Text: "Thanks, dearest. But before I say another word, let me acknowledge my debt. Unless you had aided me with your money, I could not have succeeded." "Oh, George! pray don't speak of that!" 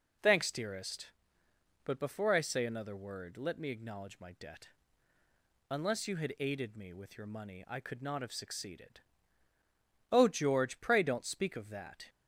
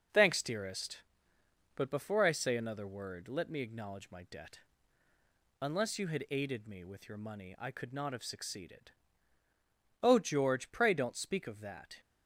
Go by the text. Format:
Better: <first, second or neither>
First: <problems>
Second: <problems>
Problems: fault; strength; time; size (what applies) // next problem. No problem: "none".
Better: first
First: none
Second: gets quieter; noticeable; throughout; 4.5 dB